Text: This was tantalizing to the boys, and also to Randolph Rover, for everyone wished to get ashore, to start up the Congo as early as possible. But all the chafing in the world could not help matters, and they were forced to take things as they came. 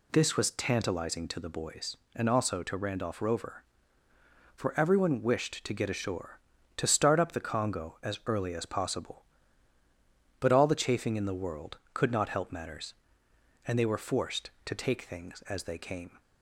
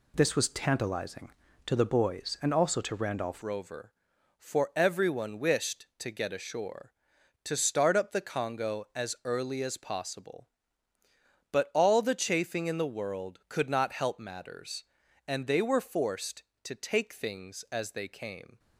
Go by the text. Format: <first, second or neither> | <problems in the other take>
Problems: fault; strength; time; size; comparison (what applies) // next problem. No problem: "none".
first | changes voice at "Rover"; from 3.4 s on; 15.1 s long